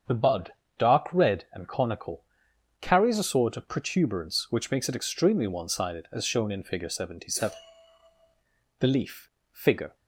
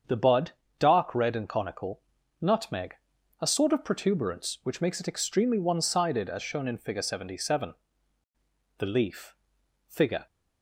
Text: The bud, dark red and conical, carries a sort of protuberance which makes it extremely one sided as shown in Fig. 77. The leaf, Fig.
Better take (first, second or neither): first